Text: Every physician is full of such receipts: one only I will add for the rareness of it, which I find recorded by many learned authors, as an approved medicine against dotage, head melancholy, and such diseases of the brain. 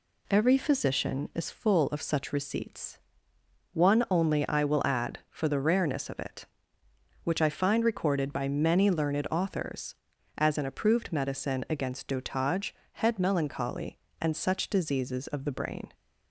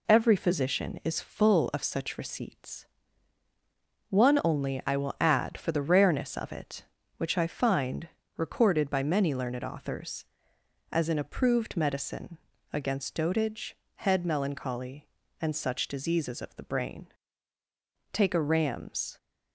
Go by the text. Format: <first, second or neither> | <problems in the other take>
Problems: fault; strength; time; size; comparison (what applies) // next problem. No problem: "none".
first | pauses between "find" and "recorded"; slight; at 8.0 s; 0.30 s long // pauses between "medicine" and "against"; slight; at 12.3 s; 0.34 s long // goes on to say "Take a ram's"; noticeable; from 18.1 s on; 1.0 s long